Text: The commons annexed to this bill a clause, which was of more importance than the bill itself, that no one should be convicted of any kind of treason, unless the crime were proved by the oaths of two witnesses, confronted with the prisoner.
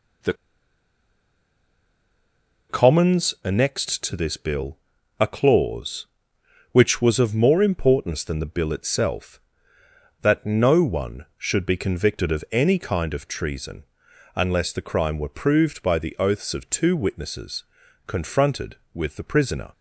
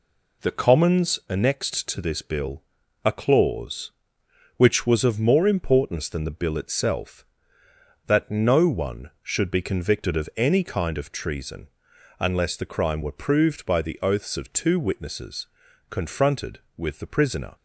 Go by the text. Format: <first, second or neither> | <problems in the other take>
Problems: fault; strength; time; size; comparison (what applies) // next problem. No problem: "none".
second | pauses between "The" and "commons"; strong; at 0.3 s; 2.3 s long // pauses between "bill" and "a"; at 4.7 s; 0.40 s long; also in the second